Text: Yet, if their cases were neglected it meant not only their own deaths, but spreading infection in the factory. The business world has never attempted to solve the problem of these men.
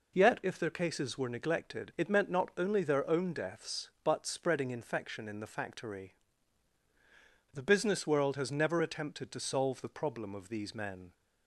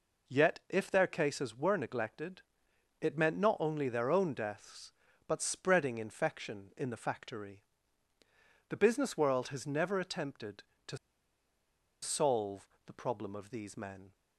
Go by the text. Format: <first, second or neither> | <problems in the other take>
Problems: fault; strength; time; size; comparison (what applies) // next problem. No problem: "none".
first | pauses between "neglected" and "it"; noticeable; at 2.4 s; 0.60 s long // pauses between "to" and "solve"; at 10.9 s; 1.0 s long // pauses between "solve" and "the"; slight; at 12.6 s; 0.20 s long